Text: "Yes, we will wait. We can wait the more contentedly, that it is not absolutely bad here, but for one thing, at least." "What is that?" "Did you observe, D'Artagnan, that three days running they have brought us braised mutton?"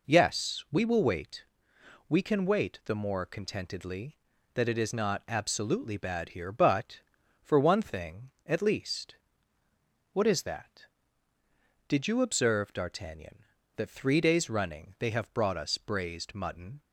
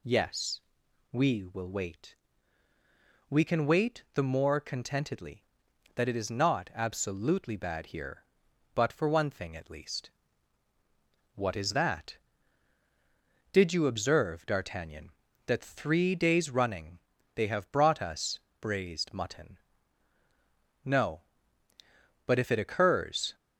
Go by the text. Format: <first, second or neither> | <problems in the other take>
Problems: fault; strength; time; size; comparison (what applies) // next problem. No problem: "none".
first | pauses between "running" and "they"; slight; at 16.9 s; 0.36 s long // pauses between "us" and "braised"; slight; at 18.4 s; 0.18 s long // goes on to say "No but if it occurs"; strong; from 20.8 s on; 2.5 s long